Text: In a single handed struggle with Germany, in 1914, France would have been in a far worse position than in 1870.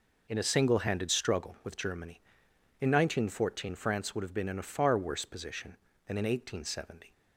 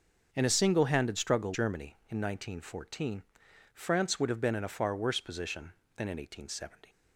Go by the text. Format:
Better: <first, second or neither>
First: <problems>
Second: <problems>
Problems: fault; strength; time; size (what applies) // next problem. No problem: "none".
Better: first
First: none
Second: starts louder than the rest; until 1.3 s; 6.5 dB // skips "with"; at 1.5 s